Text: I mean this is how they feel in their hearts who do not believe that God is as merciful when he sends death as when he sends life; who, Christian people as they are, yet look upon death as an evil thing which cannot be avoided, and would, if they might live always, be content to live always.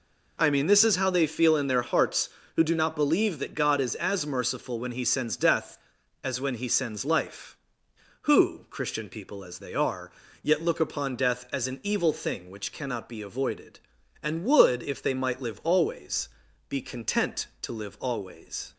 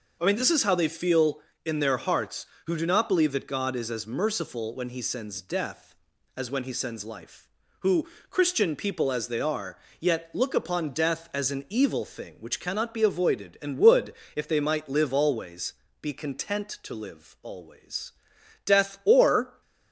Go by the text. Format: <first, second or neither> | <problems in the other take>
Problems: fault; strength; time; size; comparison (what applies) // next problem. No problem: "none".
first | goes on to say "Death or"; noticeable; from 18.6 s on; 0.96 s long